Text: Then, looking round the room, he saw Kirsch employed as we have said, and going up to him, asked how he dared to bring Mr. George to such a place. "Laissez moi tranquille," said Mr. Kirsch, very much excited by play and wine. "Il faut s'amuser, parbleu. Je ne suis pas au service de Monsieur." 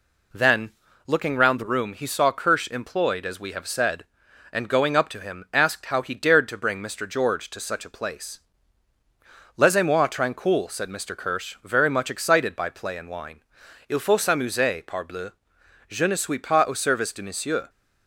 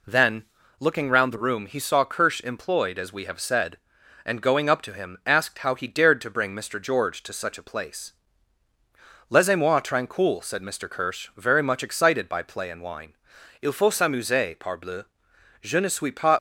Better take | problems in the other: first | stops before "au service de Monsieur"; at 16.3 s

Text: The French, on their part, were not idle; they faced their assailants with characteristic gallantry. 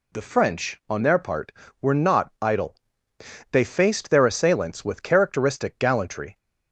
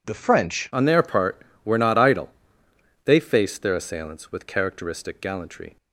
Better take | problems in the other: first | changes voice at "on"; from 0.7 s on; 5.0 s long

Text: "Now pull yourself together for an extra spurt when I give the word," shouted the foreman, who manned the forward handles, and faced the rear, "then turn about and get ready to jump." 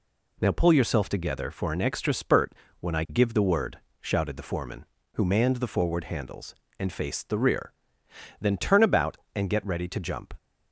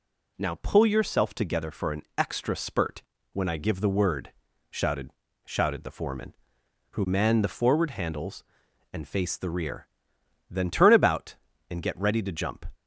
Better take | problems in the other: first | pauses between "an" and "extra"; slight; at 2.0 s; 0.16 s long // pauses between "spurt" and "when"; slight; at 3.0 s; 0.30 s long; slight in the first // says "shouted" twice; at 5.4 s

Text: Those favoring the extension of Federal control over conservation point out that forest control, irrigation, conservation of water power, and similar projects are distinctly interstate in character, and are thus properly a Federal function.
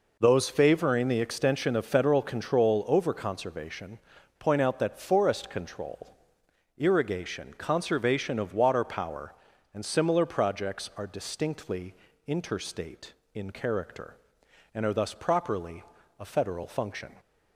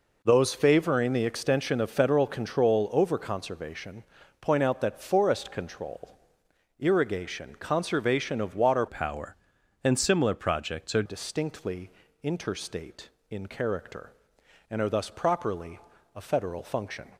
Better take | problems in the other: first | pauses between "conservation" and "point"; slight; at 4.0 s; 0.36 s long; also in the first // changes voice from "power" to "are"; from 8.8 to 11.0 s; 2.2 s long // pauses between "distinctly" and "interstate"; slight; at 11.9 s; 0.32 s long; slight in the first // pauses between "properly" and "a"; slight; at 15.7 s; 0.36 s long; slight in the first

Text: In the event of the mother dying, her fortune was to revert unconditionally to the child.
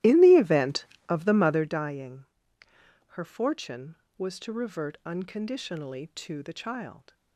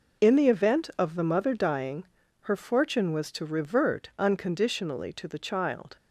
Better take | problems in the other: second | starts louder than the rest; strong; until 1.8 s; 15 dB

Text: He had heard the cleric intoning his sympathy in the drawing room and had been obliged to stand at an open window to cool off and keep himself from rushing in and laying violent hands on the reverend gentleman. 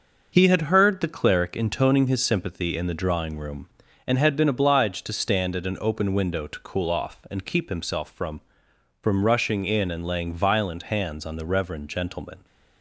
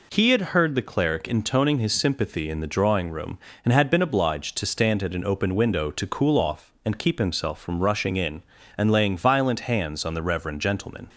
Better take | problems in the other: second | says "from" twice; at 9.0 s

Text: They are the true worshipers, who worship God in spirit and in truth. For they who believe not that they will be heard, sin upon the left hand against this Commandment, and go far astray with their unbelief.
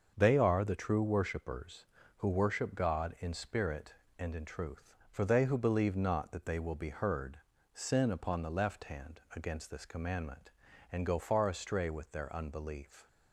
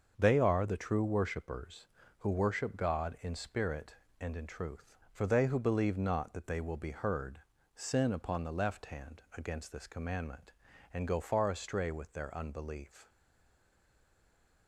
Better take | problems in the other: first | starts louder than the rest; until 1.1 s; 6.5 dB; also in the first // stays silent after the last word; noticeable; from 13.0 s on; 1.6 s long

